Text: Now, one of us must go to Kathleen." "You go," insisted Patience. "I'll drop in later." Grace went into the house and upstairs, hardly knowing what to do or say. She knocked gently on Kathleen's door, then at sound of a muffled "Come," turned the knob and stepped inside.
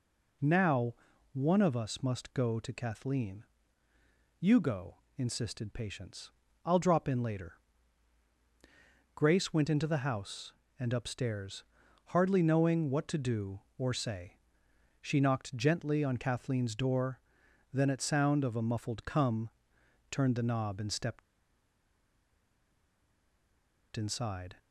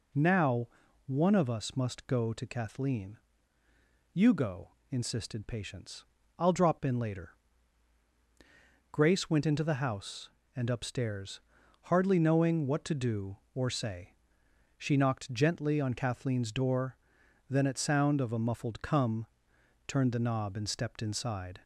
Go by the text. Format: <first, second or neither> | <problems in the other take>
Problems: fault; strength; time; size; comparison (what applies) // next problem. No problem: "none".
second | pauses between "stepped" and "inside"; strong; at 21.2 s; 2.7 s long